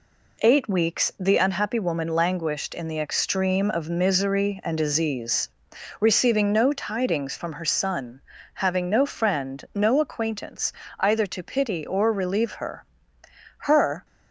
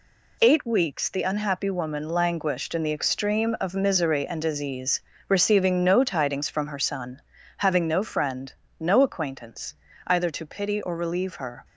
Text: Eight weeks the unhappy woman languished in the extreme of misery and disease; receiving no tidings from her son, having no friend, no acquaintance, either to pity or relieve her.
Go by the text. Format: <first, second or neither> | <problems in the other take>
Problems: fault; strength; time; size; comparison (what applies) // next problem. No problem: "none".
second | goes on to say "Her"; slight; from 13.5 s on; 0.46 s long